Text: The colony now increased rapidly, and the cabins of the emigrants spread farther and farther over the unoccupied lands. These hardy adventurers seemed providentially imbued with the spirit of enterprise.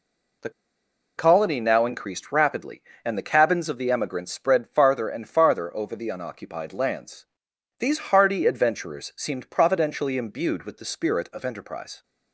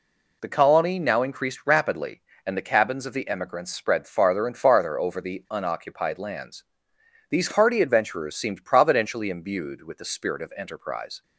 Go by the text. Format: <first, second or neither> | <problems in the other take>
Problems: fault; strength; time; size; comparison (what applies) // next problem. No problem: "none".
second | pauses between "The" and "colony"; noticeable; at 0.4 s; 0.67 s long